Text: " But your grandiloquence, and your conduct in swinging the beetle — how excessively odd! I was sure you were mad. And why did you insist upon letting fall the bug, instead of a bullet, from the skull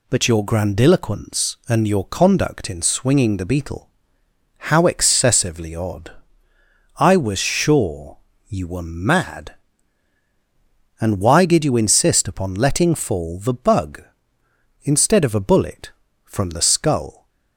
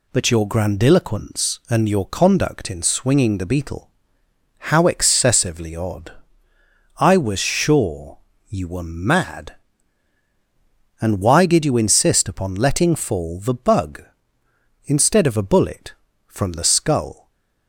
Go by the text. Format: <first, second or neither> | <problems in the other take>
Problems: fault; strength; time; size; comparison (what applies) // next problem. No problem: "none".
neither | pauses between "sure" and "you"; slight; the same in both